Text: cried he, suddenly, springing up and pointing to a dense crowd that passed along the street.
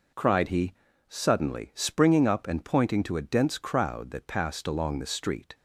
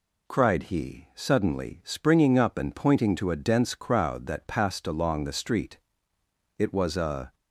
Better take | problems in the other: first | goes on to say "It was a"; noticeable; from 6.5 s on; 0.76 s long

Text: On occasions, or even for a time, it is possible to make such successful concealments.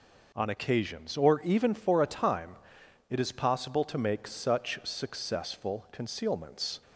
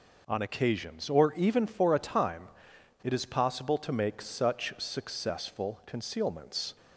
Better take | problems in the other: neither | none

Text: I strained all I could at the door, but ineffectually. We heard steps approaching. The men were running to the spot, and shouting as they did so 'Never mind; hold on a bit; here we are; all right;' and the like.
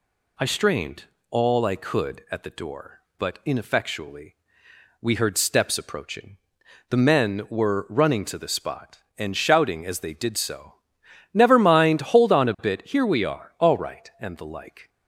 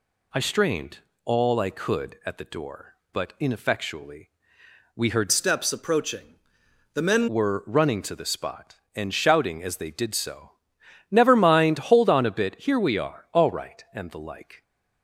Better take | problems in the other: first | pauses between "strained" and "all"; slight; at 0.9 s; 0.26 s long; slight in the first // changes voice from "steps" to "men"; from 5.3 to 7.2 s; 1.9 s long // pauses between "so" and "Never"; noticeable; at 10.5 s; 0.58 s long; noticeable in the first

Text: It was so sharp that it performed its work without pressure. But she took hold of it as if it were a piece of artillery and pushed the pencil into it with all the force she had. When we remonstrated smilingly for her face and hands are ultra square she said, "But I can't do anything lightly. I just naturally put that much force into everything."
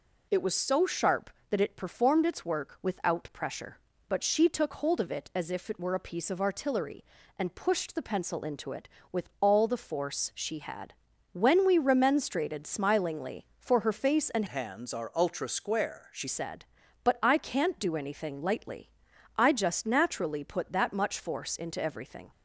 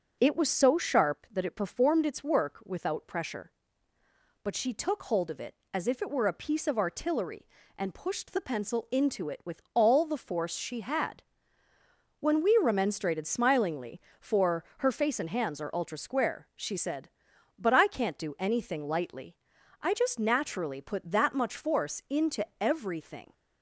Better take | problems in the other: second | changes voice from "hands" to "she"; from 14.4 to 16.2 s; 1.8 s long

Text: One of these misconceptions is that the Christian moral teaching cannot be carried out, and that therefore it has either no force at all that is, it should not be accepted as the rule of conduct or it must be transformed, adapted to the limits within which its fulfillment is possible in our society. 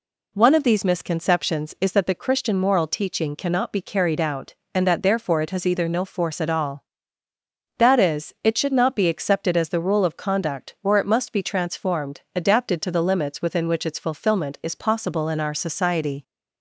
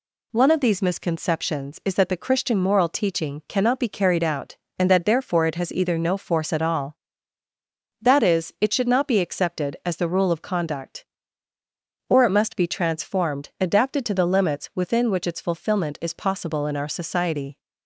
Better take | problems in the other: neither | none

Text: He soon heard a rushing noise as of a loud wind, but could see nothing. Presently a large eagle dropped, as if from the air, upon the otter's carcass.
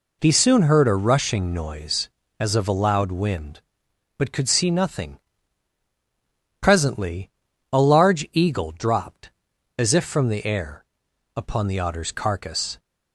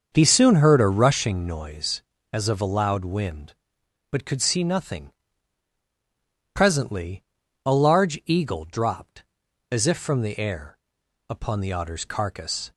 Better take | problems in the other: first | starts louder than the rest; until 1.4 s; 6.5 dB // pauses between "Presently" and "a"; at 7.2 s; 0.42 s long; also in the first

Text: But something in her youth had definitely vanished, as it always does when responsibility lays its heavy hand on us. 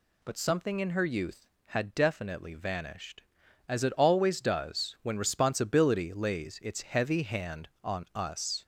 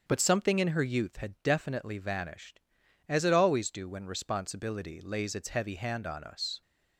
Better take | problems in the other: first | starts louder than the rest; until 1.0 s; 7 dB // says "do" for "does"; at 3.6 s

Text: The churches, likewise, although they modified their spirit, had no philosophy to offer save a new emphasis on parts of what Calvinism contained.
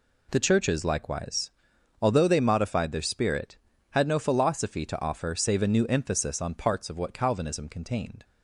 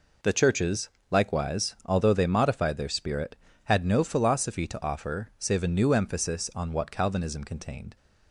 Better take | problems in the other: first | skips "parts of"; at 6.7 s

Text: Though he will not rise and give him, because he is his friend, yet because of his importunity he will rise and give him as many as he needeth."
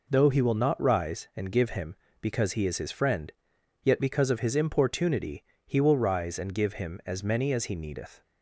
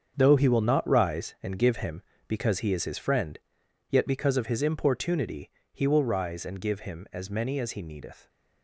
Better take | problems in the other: first | gets quieter; strong; throughout; 10 dB // pauses between "importunity" and "he"; slight; at 5.5 s; 0.22 s long; slight in the first

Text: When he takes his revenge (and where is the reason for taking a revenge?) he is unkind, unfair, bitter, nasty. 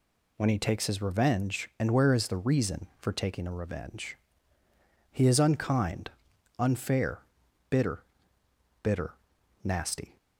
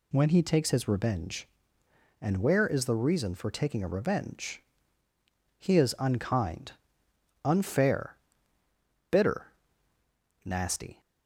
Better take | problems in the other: second | says "bitter" twice; at 8.8 s

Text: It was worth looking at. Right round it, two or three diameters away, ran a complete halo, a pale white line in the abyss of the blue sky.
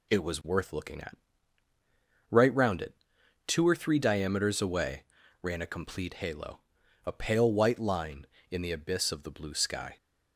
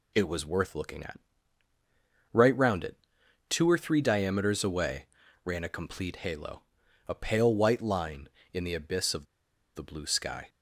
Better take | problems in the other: first | pauses between "of" and "the"; noticeable; at 9.2 s; 0.50 s long

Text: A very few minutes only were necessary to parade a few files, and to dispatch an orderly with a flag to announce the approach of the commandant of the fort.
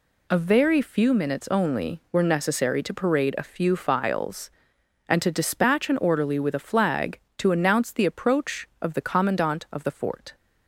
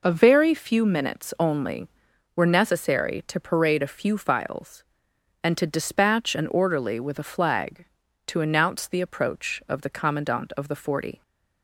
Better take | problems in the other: first | says "forty" for "fort"; at 10.7 s

